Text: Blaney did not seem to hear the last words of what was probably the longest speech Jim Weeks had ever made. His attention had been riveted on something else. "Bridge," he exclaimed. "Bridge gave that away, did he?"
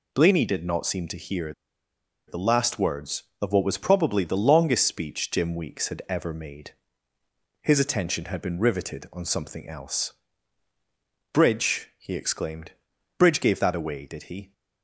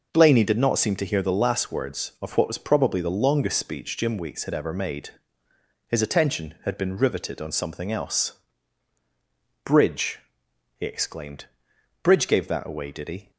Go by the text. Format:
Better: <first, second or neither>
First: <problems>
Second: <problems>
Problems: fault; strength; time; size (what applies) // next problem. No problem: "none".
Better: second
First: pauses between "hear" and "the"; noticeable; at 1.5 s; 0.74 s long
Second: none